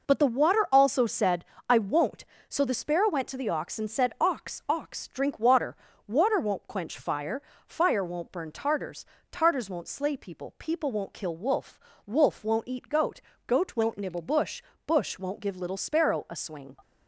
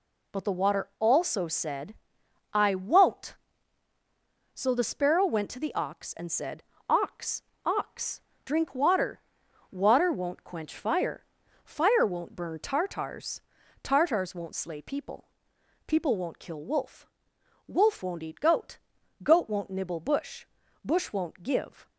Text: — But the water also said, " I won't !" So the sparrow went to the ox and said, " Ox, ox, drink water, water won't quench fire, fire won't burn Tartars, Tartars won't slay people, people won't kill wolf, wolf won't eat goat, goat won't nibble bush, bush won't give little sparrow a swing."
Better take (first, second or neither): first